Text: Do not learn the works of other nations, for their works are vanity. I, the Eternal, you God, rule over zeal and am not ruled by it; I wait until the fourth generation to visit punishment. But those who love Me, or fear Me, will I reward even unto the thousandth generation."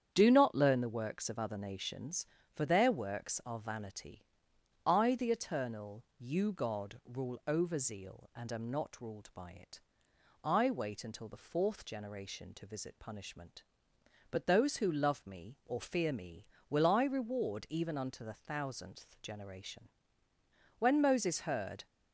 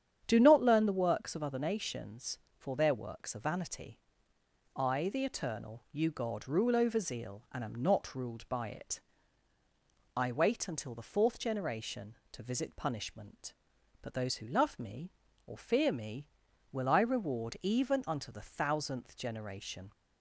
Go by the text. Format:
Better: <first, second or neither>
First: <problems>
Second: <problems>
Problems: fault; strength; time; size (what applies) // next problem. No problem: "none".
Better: second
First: starts louder than the rest; strong; until 1.1 s; 8.5 dB // goes on to say "When Moses heard"; noticeable; from 20.7 s on; 1.0 s long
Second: starts louder than the rest; strong; until 1.2 s; 8.5 dB